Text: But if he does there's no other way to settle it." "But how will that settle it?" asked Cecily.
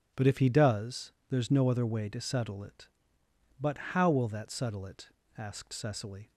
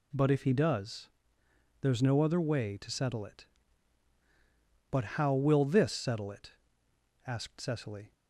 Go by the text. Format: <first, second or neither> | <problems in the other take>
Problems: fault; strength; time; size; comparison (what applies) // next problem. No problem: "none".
first | pauses between "does" and "there's"; noticeable; at 1.0 s; 0.74 s long; slight in the first // says "this" for "that"; at 5.6 s